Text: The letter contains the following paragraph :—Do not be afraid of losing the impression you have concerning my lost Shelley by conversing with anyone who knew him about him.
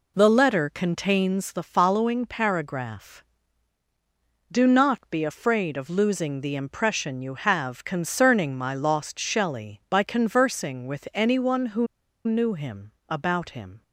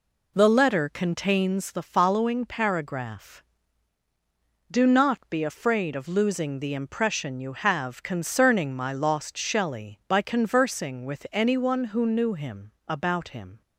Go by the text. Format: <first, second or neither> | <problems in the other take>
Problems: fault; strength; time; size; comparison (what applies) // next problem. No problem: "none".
second | pauses between "who" and "knew"; at 11.8 s; 0.39 s long // pauses between "him" and "about"; slight; at 12.9 s; 0.18 s long; slight in the second